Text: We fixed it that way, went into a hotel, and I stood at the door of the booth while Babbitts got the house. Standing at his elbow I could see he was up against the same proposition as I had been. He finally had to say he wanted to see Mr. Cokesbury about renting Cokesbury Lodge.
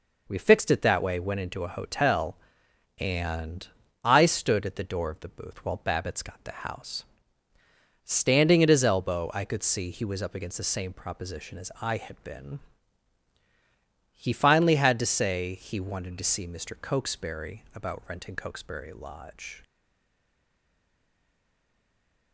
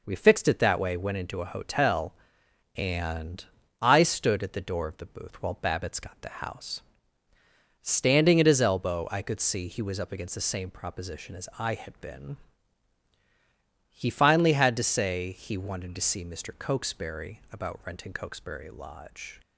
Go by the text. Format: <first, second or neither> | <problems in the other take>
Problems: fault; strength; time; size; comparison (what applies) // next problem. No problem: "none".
second | pauses between "and" and "I"; slight; at 3.6 s; 0.36 s long; slight in the second // stays silent after the last word; strong; from 19.6 s on; 2.7 s long